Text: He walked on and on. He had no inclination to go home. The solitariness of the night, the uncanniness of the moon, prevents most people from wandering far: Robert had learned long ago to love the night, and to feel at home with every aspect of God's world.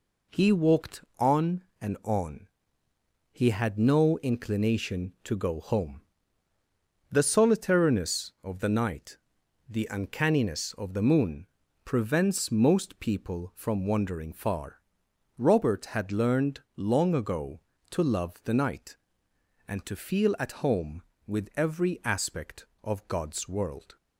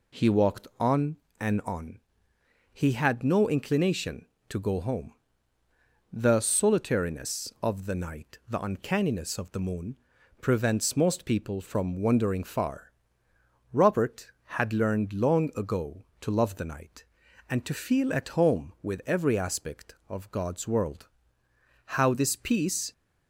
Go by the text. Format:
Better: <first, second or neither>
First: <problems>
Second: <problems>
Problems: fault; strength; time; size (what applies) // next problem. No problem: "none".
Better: first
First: none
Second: goes on to say "How this peace"; noticeable; from 21.9 s on; 0.94 s long